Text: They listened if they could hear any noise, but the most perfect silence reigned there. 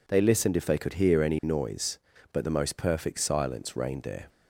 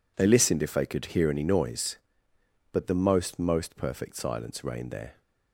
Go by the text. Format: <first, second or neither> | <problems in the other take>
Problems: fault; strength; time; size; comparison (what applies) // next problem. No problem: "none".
first | says "most" twice; at 3.3 s